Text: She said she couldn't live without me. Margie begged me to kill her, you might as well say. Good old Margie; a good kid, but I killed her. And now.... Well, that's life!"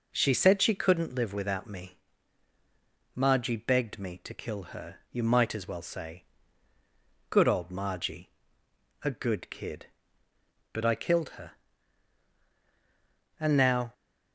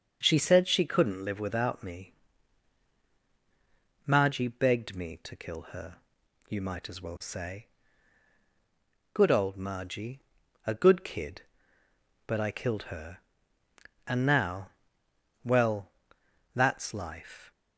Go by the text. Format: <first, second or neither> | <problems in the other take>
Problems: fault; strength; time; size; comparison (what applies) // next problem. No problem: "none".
second | stops before "Well that's life"; at 13.9 s